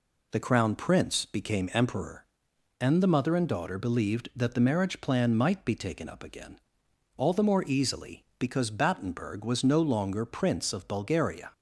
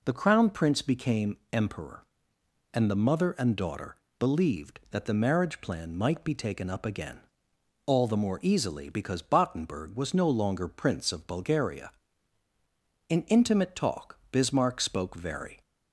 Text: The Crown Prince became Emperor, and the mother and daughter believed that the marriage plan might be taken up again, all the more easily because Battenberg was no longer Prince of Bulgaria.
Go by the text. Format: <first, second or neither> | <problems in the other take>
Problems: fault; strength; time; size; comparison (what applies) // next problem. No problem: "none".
first | pauses between "became" and "Emperor"; slight; at 1.3 s; 0.16 s long // pauses between "daughter" and "believed"; slight; at 3.9 s; 0.20 s long // goes on to say "In intimate talk Bismarck spoke very"; strong; from 13.0 s on; 2.5 s long